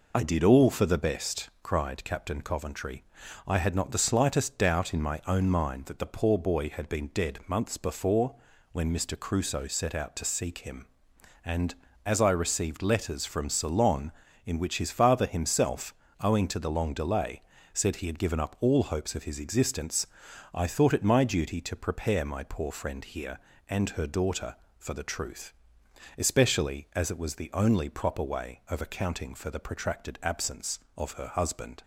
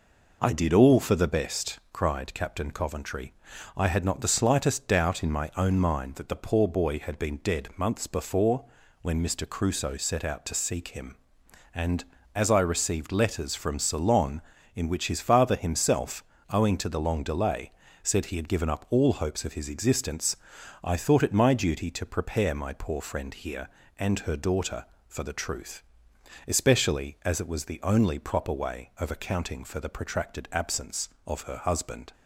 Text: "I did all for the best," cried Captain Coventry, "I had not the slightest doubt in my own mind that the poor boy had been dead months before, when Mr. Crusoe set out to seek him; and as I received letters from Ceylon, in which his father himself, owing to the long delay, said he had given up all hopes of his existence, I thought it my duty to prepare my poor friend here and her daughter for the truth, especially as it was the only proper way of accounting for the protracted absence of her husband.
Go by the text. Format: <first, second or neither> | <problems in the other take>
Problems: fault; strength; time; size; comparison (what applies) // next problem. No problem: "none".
second | loses the start of "I"; at 0.1 s; 35 ms